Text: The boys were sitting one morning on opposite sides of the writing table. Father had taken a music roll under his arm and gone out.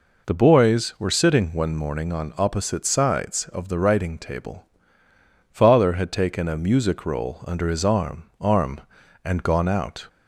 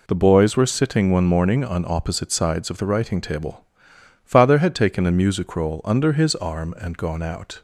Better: second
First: says "arm" twice; at 8.4 s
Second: none

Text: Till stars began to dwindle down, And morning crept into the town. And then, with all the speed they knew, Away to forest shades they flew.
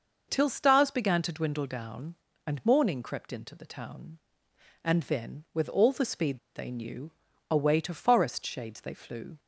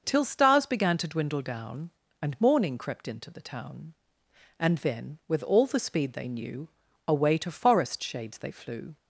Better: second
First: starts louder than the rest; noticeable; until 1.3 s; 6 dB // pauses between "speed" and "they"; slight; at 6.3 s; 0.17 s long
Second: none

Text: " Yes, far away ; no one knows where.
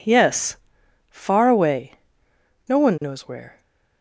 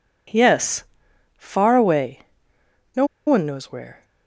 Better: first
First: none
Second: pauses between "no" and "one"; slight; at 3.0 s; 0.20 s long

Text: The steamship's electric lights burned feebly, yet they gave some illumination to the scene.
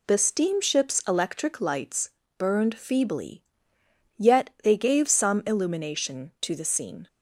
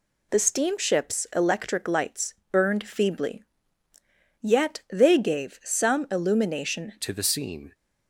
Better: first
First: pauses between "lights" and "burned"; slight; at 2.1 s; 0.26 s long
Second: pauses between "lights" and "burned"; slight; at 2.3 s; 0.16 s long // changes voice at "to"; from 7.0 s on; 0.7 s long

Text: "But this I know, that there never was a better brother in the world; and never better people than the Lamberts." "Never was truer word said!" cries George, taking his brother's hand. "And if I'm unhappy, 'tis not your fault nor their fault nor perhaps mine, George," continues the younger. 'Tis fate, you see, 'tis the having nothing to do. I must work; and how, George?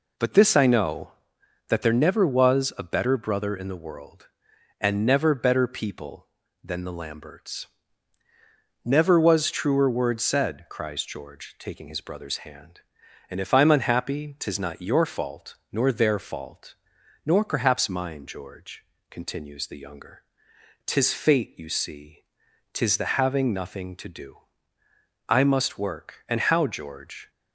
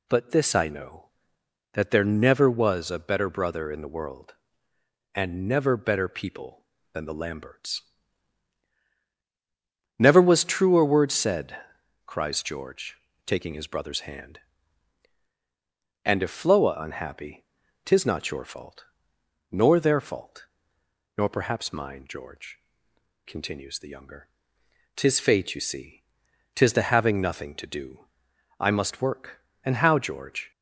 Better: first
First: pauses between "fault" and "nor"; noticeable; at 16.7 s; 0.50 s long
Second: says "Floa" for "I'm"; at 16.3 s // pauses between "fault" and "nor"; noticeable; at 18.8 s; 0.64 s long // pauses between "fault" and "nor"; noticeable; at 20.4 s; 0.70 s long

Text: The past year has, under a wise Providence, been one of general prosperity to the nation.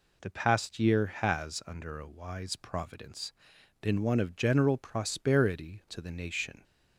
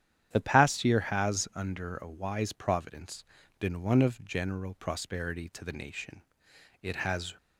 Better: first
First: none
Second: starts louder than the rest; strong; until 1.3 s; 10 dB // goes on to say "It has"; from 6.8 s on; 0.54 s long

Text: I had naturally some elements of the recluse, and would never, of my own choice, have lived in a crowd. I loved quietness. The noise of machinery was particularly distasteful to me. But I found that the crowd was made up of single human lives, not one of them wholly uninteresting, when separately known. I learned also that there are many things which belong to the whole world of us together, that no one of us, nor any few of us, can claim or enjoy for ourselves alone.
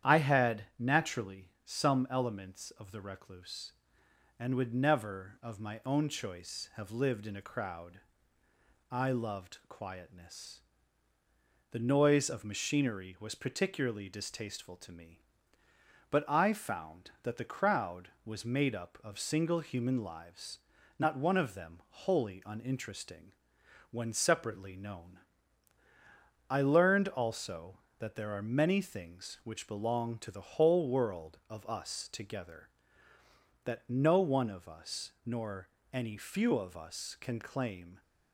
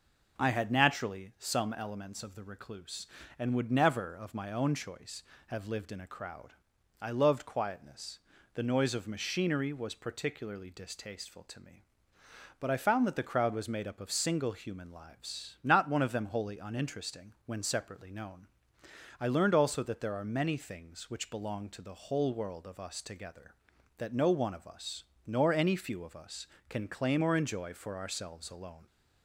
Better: second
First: starts louder than the rest; strong; until 1.1 s; 10 dB // pauses between "naturally" and "some"; slight; at 1.4 s; 0.16 s long // pauses between "nor" and "any"; slight; at 35.6 s; 0.24 s long // stops before "or enjoy for ourselves alone"; at 38.0 s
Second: none

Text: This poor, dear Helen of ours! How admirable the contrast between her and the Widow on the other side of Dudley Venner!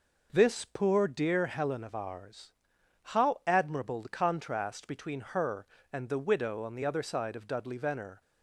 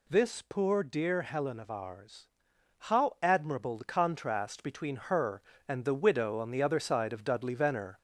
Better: first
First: none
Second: gets louder; slight; throughout; 3 dB

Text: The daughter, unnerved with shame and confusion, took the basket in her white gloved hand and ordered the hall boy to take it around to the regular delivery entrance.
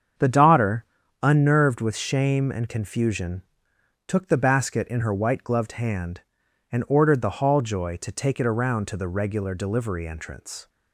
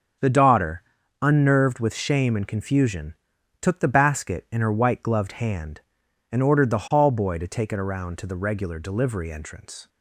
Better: second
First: starts louder than the rest; strong; until 1.5 s; 7.5 dB // says "joy" for "boy"; at 7.6 s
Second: starts louder than the rest; strong; until 1.6 s; 7 dB

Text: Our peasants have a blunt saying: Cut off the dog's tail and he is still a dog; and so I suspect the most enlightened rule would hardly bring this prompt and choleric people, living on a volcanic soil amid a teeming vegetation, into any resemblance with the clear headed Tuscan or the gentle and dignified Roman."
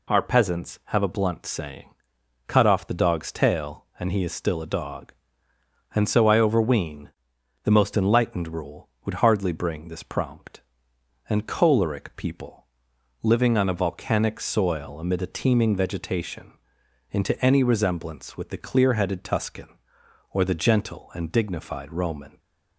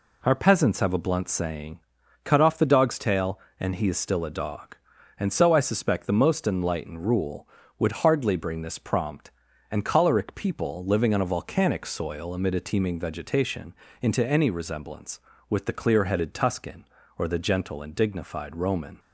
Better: second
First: says "overween" for "suspect"; at 6.3 s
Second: none

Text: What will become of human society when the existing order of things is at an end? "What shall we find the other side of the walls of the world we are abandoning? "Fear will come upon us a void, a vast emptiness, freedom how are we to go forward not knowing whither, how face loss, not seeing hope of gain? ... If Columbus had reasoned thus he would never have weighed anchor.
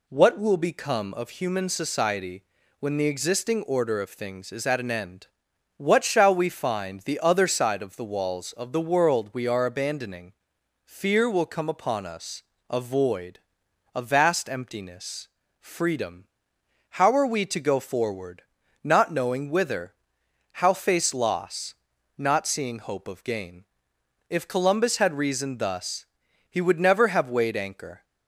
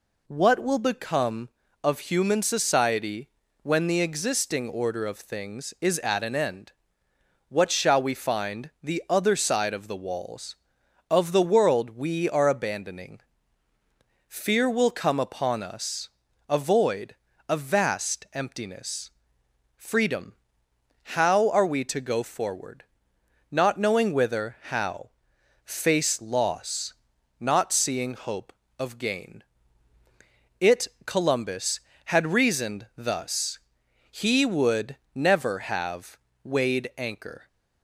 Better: first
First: pauses between "society" and "when"; slight; at 2.4 s; 0.36 s long // pauses between "us" and "a"; slight; at 12.4 s; 0.26 s long // pauses between "freedom" and "how"; noticeable; at 16.2 s; 0.62 s long // pauses between "forward" and "not"; at 18.4 s; 0.42 s long // pauses between "thus" and "he"; at 26.0 s; 0.44 s long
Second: pauses between "society" and "when"; slight; at 3.2 s; 0.34 s long // pauses between "us" and "a"; at 16.0 s; 0.40 s long // pauses between "freedom" and "how"; noticeable; at 20.3 s; 0.80 s long // pauses between "forward" and "not"; noticeable; at 22.8 s; 0.66 s long // pauses between "how" and "face"; noticeable; at 25.0 s; 0.54 s long // says "It" for "If"; at 30.5 s // pauses between "thus" and "he"; noticeable; at 33.5 s; 0.52 s long // pauses between "would" and "never"; slight; at 34.9 s; 0.16 s long // pauses between "have" and "weighed"; slight; at 36.1 s; 0.26 s long

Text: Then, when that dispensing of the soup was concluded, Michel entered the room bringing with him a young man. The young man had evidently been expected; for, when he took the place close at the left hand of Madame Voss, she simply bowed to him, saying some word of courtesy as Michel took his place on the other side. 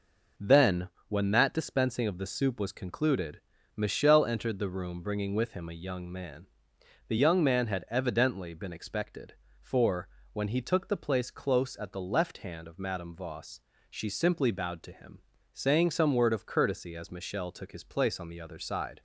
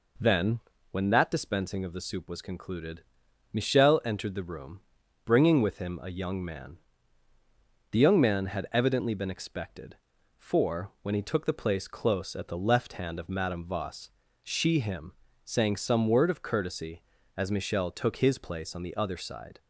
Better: first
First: none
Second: pauses between "room" and "bringing"; at 4.8 s; 0.44 s long // skips "simply bowed to"; at 14.7 s

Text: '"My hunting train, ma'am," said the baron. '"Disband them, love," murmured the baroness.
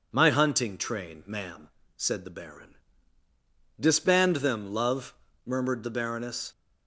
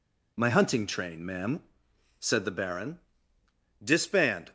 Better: first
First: none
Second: stops before "them love murmured the baroness"; at 4.4 s

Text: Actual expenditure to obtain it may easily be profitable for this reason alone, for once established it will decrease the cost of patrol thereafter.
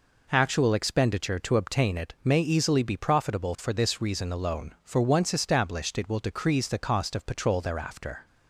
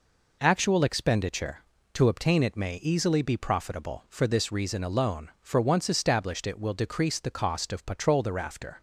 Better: neither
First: none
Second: none

